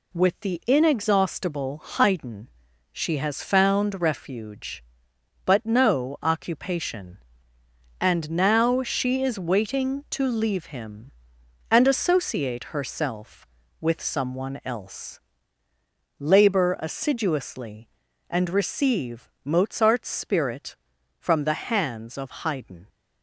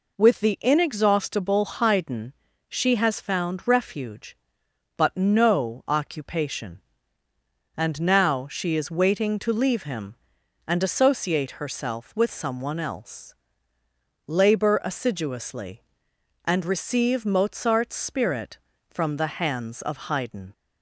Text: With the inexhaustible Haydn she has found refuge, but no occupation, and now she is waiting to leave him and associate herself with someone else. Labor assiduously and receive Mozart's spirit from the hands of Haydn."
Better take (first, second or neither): neither